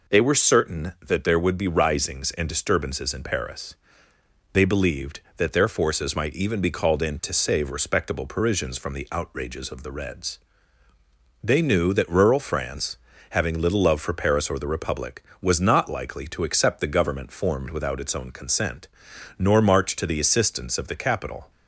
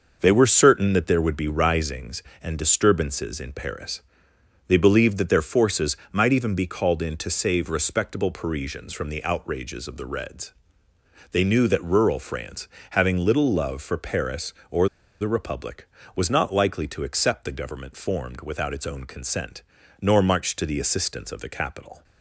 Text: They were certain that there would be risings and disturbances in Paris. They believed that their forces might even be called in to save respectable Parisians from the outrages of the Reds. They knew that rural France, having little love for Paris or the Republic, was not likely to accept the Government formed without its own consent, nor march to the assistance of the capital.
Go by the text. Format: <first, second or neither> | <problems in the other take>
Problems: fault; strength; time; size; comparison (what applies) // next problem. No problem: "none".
first | pauses between "forces" and "might"; slight; at 5.9 s; 0.16 s long // pauses between "or" and "the"; slight; at 14.8 s; 0.33 s long